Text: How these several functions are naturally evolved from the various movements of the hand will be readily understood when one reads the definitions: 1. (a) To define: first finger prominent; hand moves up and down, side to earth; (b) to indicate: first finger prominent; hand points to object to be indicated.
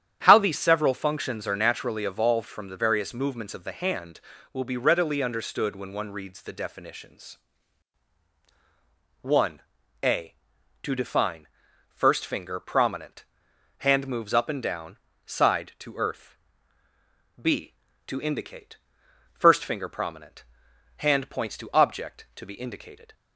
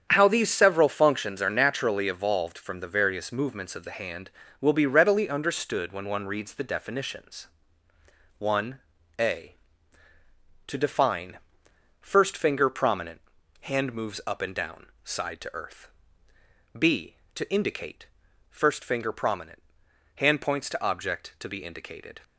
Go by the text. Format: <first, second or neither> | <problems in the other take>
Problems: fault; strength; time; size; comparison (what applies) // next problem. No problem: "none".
neither | starts louder than the rest; strong; the same in both